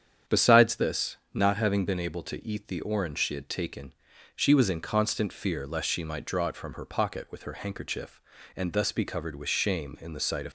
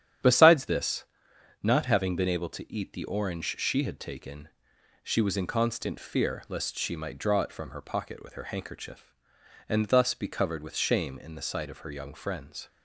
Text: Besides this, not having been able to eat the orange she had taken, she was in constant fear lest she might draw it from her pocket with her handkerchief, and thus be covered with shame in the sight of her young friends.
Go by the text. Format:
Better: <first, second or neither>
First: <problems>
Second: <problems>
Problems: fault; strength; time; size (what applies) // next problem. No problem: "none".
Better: second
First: starts louder than the rest; strong; until 1.4 s; 8.5 dB // stops before "her young friends"; at 10.4 s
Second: starts louder than the rest; strong; until 1.8 s; 9.5 dB